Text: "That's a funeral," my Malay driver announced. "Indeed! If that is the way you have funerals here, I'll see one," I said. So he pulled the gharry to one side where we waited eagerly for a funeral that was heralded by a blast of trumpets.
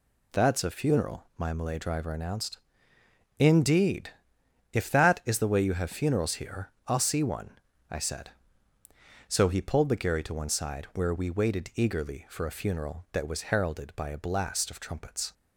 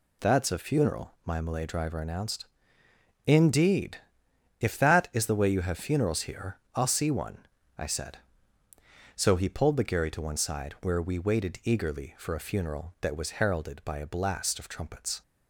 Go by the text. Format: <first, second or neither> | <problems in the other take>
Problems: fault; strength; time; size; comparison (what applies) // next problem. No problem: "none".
neither | none